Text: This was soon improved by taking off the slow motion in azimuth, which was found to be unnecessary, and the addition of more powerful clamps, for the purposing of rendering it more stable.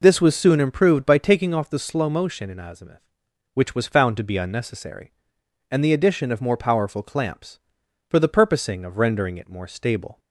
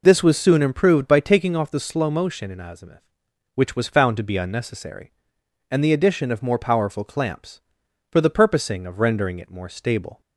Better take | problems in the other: neither | none

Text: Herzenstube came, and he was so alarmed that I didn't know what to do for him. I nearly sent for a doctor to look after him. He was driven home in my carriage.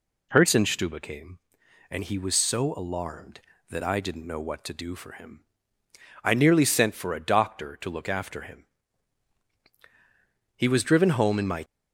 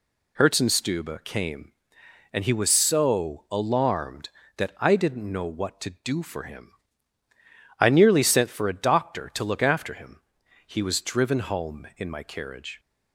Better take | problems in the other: second | stops before "carriage"; at 11.6 s

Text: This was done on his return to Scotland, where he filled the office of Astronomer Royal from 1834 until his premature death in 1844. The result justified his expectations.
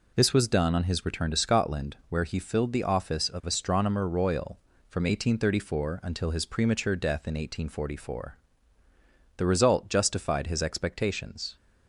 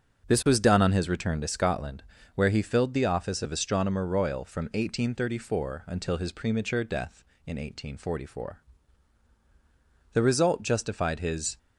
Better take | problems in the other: first | starts louder than the rest; until 1.3 s; 7 dB // stops before "expectations"; at 11.5 s

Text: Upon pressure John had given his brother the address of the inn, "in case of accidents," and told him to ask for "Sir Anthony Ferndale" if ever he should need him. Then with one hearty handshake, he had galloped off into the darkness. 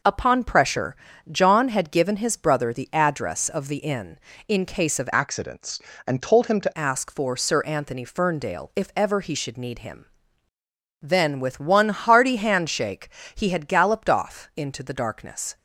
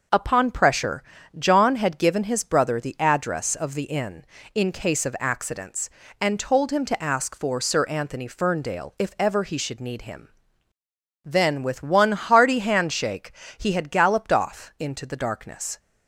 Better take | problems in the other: second | pauses between "pressure" and "John"; slight; at 0.9 s; 0.34 s long; slight in the second // changes voice from "accidents" to "to"; from 5.1 to 6.7 s; 1.6 s long

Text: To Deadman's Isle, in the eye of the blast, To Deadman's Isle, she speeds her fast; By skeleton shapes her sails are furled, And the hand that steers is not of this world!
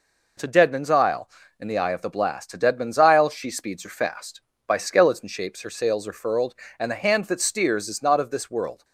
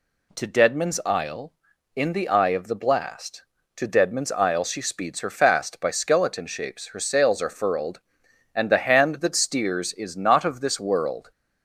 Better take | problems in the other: neither | none

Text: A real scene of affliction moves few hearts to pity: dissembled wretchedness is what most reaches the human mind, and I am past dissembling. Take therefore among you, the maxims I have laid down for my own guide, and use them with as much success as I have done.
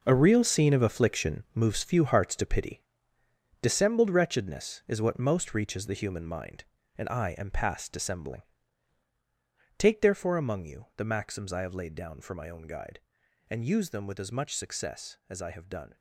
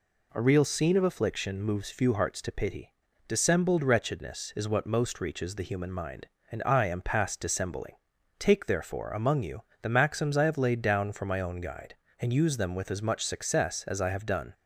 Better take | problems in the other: second | gets quieter; strong; throughout; 11.5 dB

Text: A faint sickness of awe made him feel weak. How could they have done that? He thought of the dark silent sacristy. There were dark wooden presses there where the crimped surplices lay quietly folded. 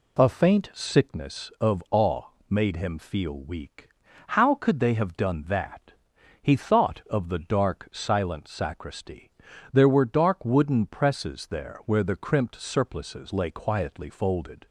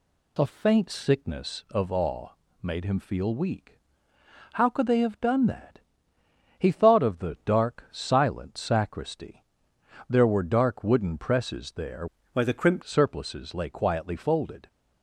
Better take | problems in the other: first | pauses between "awe" and "made"; slight; at 2.2 s; 0.32 s long; slight in the first // changes voice from "where" to "crimped"; from 12.3 to 12.8 s; 0.5 s long

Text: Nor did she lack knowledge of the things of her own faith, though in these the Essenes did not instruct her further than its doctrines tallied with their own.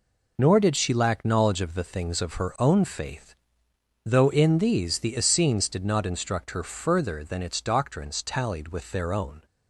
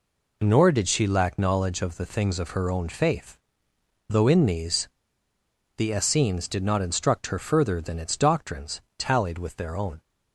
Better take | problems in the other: first | pauses between "these" and "the"; noticeable; at 4.8 s; 0.89 s long // pauses between "doctrines" and "tallied"; slight; at 8.7 s; 0.20 s long

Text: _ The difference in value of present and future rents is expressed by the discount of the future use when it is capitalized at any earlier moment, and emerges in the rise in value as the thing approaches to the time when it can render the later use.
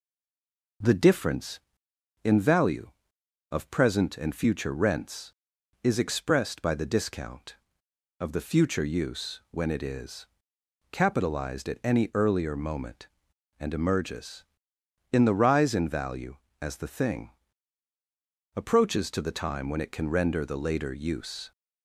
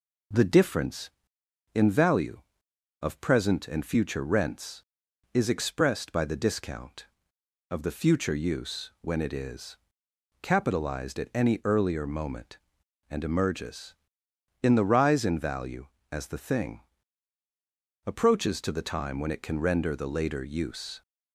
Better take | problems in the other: second | stays silent before the first word; slight; until 0.8 s; 0.8 s long // pauses between "is" and "capitalized"; noticeable; at 10.2 s; 0.66 s long; noticeable in the second // pauses between "thing" and "approaches"; strong; at 17.2 s; 1.2 s long; strong in the second

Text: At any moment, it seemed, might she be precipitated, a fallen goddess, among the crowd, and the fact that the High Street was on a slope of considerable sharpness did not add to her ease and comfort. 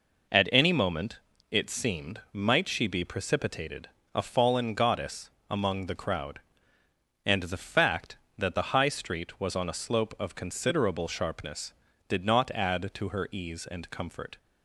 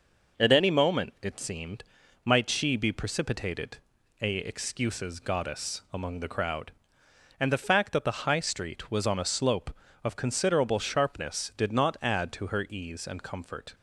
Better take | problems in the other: first | says "excuses" for "fallen"; at 4.3 s

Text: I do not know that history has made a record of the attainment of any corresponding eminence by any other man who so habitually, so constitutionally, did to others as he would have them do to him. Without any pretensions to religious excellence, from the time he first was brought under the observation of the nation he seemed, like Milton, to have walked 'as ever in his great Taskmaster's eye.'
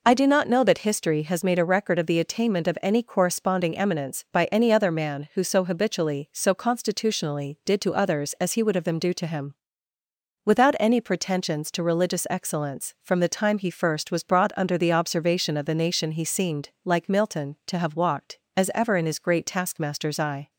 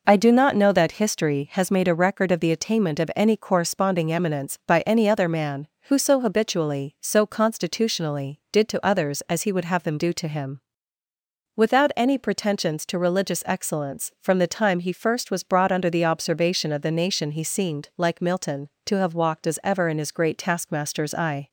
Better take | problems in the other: neither | none

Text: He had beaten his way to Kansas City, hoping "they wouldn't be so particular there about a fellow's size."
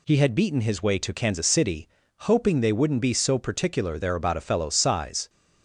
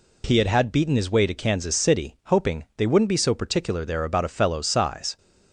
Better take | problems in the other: first | says "had" twice; at 0.4 s

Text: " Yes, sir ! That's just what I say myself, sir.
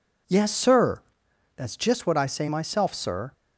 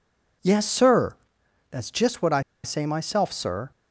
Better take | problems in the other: first | pauses between "I" and "say"; slight; at 2.3 s; 0.23 s long

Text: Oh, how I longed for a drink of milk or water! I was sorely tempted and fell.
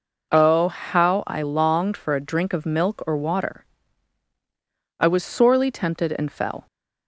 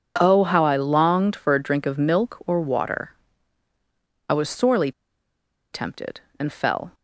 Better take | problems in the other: first | pauses between "sorely" and "tempted"; noticeable; at 4.9 s; 0.82 s long

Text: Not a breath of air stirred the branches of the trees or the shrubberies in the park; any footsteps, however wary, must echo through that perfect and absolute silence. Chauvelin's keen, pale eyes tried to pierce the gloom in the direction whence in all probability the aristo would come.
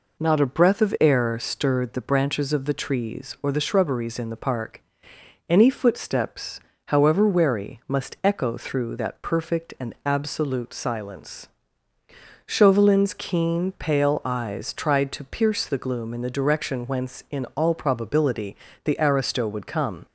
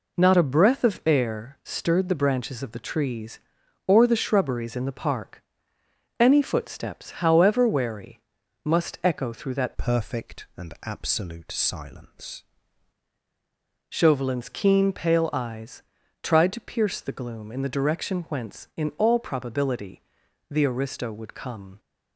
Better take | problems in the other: first | changes voice from "perfect" to "silence"; from 9.7 to 12.4 s; 2.7 s long // pauses between "eyes" and "tried"; at 15.8 s; 0.40 s long // pauses between "probability" and "the"; noticeable; at 20.0 s; 0.48 s long; slight in the first

